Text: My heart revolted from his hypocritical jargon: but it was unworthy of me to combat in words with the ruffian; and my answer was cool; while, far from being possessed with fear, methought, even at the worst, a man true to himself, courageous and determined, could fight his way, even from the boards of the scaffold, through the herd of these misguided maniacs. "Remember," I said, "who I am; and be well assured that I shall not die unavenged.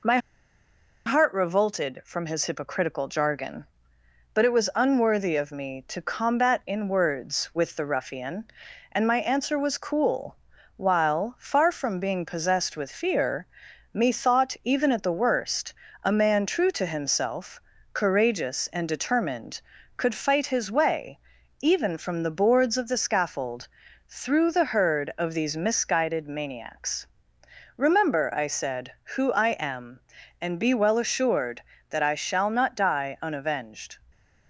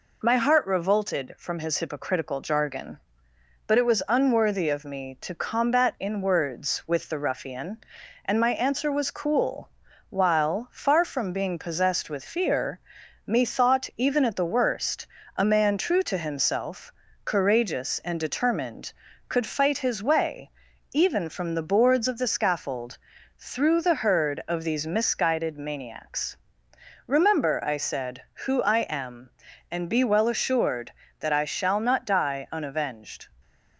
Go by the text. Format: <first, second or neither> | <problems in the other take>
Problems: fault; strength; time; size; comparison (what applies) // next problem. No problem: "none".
second | pauses between "My" and "heart"; noticeable; at 0.1 s; 0.88 s long